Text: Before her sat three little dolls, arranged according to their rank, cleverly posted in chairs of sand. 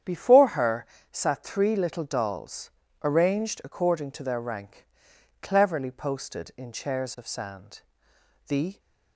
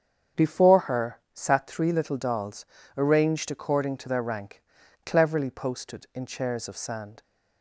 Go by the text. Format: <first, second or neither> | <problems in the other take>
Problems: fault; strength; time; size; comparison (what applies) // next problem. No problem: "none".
second | starts louder than the rest; strong; until 1.3 s; 9 dB; strong in the second // pauses between "her" and "sat"; slight; at 0.8 s; 0.28 s long; slight in the second // goes on to say "The"; slight; from 8.4 s on; 0.32 s long